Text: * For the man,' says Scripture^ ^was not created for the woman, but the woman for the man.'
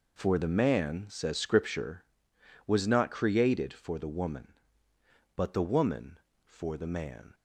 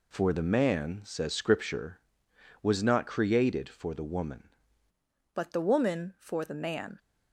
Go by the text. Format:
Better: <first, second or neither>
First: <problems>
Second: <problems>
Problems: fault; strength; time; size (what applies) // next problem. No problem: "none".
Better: first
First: none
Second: changes voice at "but"; from 5.3 s on; 1.6 s long